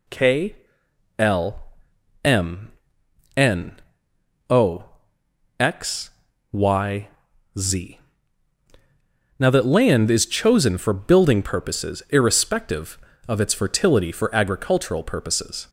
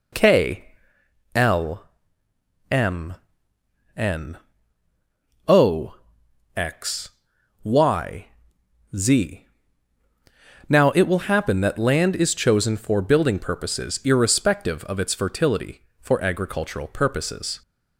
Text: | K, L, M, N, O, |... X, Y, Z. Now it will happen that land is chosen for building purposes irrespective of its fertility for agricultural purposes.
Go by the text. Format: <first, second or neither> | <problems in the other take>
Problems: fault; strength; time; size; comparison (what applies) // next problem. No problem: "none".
second | skips "it will happen"; at 9.4 s